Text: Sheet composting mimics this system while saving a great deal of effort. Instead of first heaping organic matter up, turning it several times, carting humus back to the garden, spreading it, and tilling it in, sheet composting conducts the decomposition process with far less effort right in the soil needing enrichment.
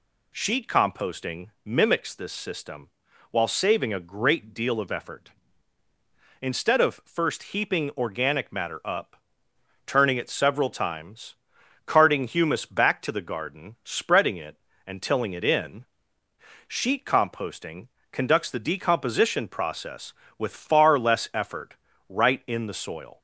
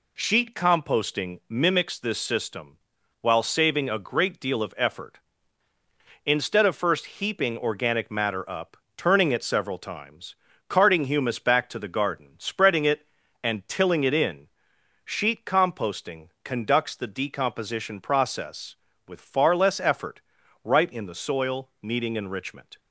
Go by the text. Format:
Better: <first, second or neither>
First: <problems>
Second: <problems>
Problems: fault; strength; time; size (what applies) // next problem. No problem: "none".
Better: second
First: pauses between "system" and "while"; at 2.8 s; 0.42 s long // pauses between "composting" and "conducts"; slight; at 17.8 s; 0.24 s long // pauses between "effort" and "right"; slight; at 21.7 s; 0.34 s long // stops before "needing enrichment"; at 23.1 s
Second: pauses between "system" and "while"; at 2.7 s; 0.44 s long // pauses between "effort" and "right"; at 20.2 s; 0.44 s long